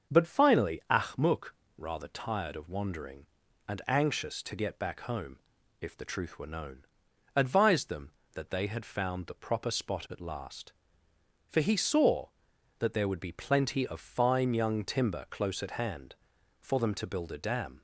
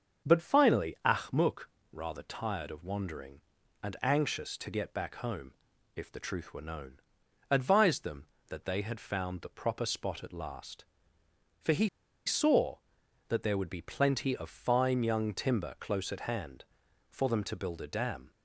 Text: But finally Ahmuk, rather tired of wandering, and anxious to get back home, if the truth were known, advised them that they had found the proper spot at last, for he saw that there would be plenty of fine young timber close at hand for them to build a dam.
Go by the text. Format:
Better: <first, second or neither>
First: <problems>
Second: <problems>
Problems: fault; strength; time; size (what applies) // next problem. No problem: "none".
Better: first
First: starts louder than the rest; until 1.2 s; 6.5 dB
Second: starts louder than the rest; until 1.3 s; 6.5 dB // pauses between "he" and "saw"; at 11.8 s; 0.37 s long